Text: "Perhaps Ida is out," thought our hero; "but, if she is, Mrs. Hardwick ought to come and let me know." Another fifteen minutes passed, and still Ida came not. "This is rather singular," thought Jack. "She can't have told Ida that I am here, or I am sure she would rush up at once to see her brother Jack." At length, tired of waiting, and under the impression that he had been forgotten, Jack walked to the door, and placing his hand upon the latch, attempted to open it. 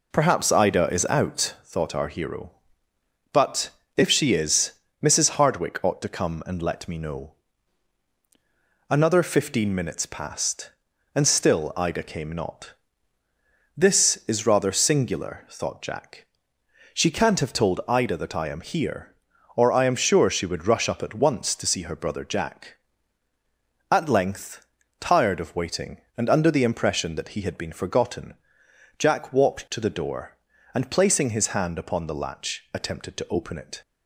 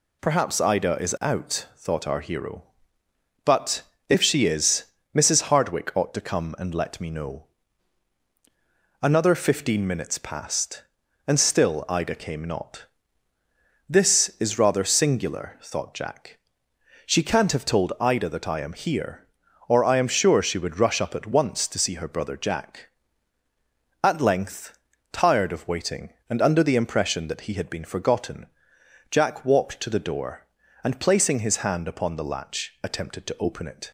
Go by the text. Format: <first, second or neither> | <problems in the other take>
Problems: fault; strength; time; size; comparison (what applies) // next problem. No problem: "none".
second | starts louder than the rest; until 1.7 s; 3.5 dB